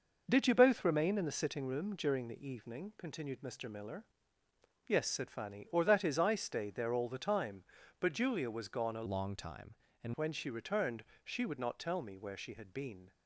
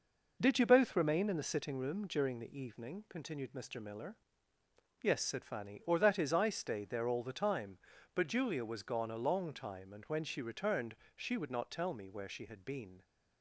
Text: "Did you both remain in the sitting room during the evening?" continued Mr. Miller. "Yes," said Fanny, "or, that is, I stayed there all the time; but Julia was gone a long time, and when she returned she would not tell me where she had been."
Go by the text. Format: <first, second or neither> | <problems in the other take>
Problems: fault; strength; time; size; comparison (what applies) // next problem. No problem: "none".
second | changes voice from "long" to "and"; from 9.0 to 10.1 s; 1.1 s long // pauses between "returned" and "she"; slight; at 11.0 s; 0.20 s long; slight in the second